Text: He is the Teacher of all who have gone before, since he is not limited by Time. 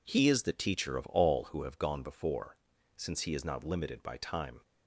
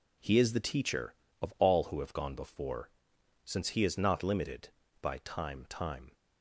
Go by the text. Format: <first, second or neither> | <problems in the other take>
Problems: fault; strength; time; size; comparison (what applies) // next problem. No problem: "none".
first | says "Time" twice; at 5.6 s